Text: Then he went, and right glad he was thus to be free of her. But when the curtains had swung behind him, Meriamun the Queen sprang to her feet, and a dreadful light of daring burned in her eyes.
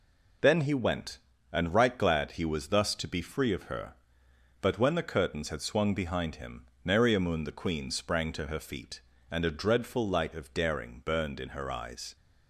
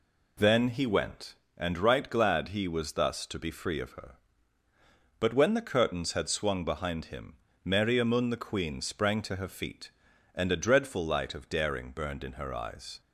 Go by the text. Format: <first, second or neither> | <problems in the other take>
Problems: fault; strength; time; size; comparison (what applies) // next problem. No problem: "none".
neither | none